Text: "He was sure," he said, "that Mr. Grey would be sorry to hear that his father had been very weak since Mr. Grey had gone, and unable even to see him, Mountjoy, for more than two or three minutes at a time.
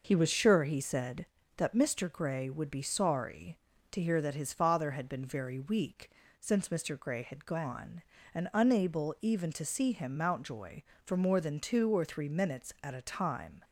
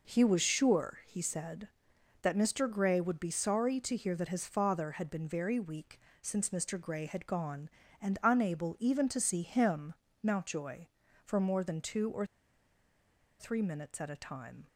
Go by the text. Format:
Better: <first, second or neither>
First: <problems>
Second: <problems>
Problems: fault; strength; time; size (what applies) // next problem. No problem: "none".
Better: first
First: pauses between "weak" and "since"; slight; at 6.1 s; 0.30 s long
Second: pauses between "weak" and "since"; slight; at 5.9 s; 0.22 s long // pauses between "or" and "three"; at 12.2 s; 1.1 s long